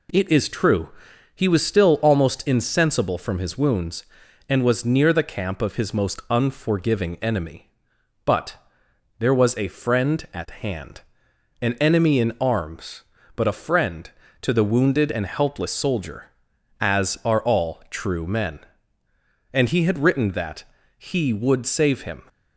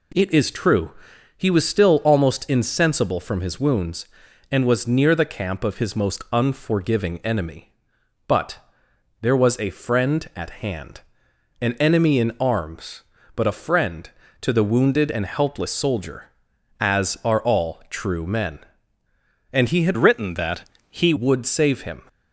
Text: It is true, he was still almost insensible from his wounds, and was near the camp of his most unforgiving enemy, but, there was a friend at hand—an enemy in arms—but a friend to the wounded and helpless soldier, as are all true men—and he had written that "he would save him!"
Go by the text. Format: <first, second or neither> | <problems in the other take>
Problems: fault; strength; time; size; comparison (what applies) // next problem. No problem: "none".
first | changes voice from "written" to "he"; from 19.9 to 21.1 s; 1.2 s long // pauses between "that" and "he"; slight; at 20.6 s; 0.28 s long; slight in the first